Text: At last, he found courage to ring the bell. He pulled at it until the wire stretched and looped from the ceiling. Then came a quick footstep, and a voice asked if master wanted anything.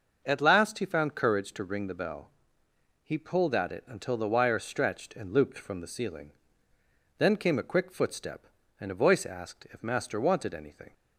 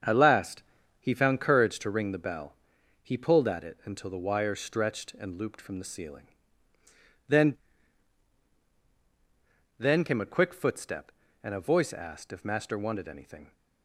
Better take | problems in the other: first | starts louder than the rest; until 1.4 s; 7 dB; noticeable in the first // says "Then" twice; at 9.7 s

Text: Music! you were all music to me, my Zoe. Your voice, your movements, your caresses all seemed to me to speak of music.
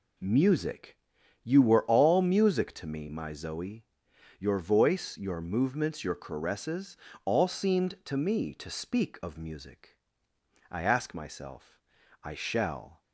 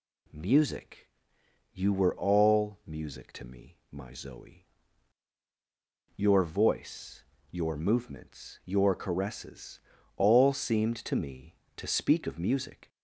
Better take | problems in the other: second | pauses between "caresses" and "all"; slight; at 6.9 s; 0.30 s long; also in the second // goes on to say "I ask myself I shall"; strong; from 10.7 s on; 2.3 s long

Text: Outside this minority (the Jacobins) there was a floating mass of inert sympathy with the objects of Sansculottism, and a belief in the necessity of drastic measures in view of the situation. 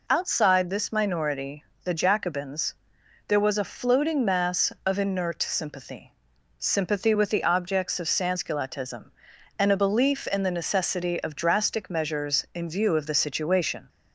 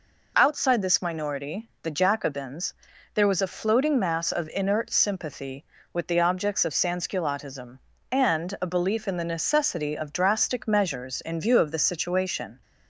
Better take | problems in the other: second | says "sympathy" twice; at 6.5 s

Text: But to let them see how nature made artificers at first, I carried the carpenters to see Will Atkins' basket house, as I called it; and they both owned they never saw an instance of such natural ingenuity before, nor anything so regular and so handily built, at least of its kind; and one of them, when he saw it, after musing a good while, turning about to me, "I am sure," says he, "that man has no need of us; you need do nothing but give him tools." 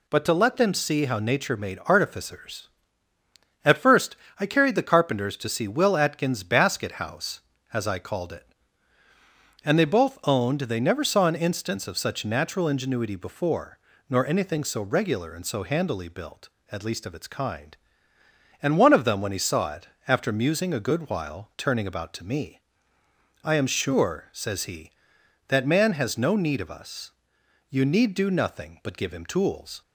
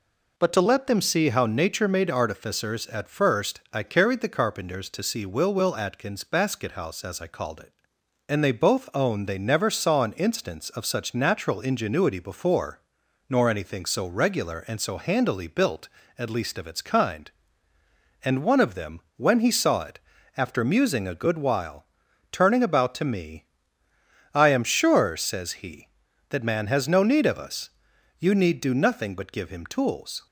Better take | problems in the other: first | says "Will" twice; at 5.5 s

